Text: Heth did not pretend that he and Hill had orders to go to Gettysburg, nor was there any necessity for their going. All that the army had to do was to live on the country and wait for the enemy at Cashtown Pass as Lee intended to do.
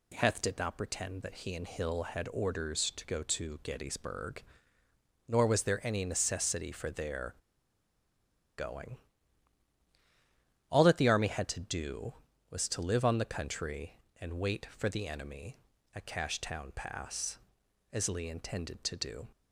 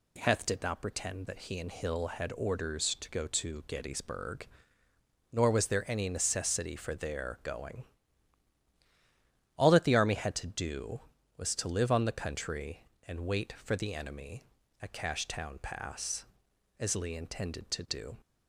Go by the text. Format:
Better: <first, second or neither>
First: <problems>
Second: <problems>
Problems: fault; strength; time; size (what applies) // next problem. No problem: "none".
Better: second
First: pauses between "their" and "going"; at 7.3 s; 1.2 s long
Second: none